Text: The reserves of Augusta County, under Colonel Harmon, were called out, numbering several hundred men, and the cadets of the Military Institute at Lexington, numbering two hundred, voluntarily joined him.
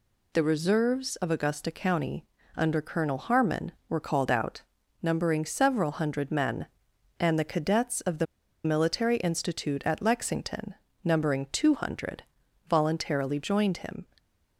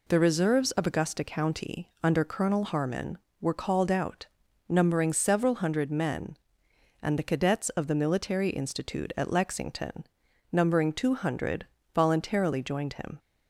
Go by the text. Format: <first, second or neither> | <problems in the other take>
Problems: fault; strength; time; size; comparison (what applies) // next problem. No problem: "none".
second | pauses between "the" and "Military"; at 8.2 s; 0.39 s long